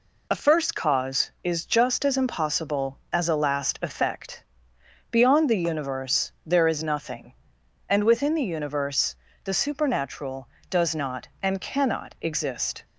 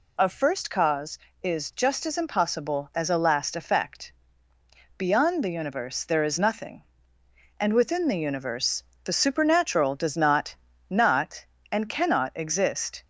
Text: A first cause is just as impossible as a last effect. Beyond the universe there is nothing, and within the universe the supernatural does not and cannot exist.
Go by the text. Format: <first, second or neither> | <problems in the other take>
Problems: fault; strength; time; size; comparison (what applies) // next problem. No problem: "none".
first | pauses between "universe" and "the"; slight; at 8.8 s; 0.22 s long; slight in the first // says "not" twice; at 10.8 s